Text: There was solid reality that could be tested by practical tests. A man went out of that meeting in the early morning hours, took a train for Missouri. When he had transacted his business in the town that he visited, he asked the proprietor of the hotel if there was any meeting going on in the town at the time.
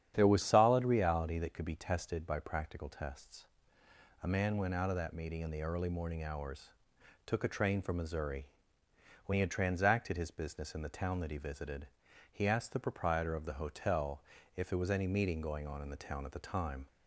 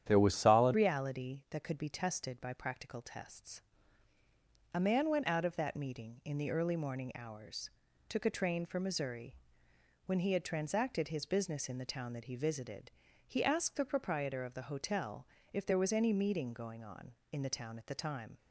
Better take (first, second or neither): first